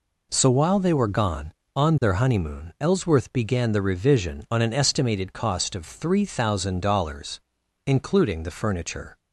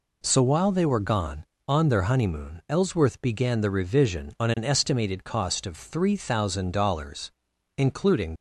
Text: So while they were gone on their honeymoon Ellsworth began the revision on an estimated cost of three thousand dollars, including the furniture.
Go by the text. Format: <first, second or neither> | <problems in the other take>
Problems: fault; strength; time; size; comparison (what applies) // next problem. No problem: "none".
first | stops before "the furniture"; at 8.3 s